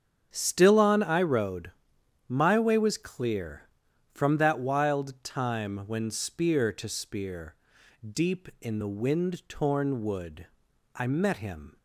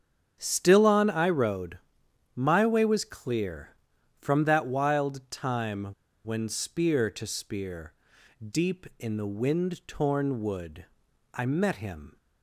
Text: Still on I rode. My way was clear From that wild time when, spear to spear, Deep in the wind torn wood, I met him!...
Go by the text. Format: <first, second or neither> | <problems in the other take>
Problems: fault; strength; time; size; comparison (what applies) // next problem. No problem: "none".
first | starts louder than the rest; strong; until 1.4 s; 7.5 dB; strong in the first // pauses between "time" and "when"; at 5.8 s; 0.38 s long